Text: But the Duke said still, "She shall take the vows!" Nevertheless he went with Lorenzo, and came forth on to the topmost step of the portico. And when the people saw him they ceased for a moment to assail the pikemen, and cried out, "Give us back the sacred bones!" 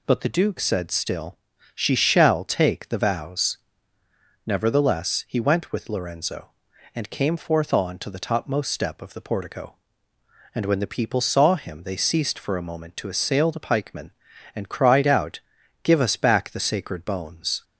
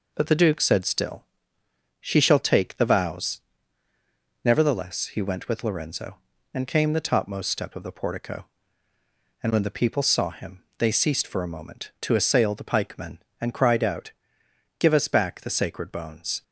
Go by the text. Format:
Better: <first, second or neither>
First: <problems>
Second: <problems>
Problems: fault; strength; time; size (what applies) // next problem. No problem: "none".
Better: first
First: none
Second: skips "forth on to"; at 6.9 s // pauses between "him" and "they"; slight; at 10.6 s; 0.18 s long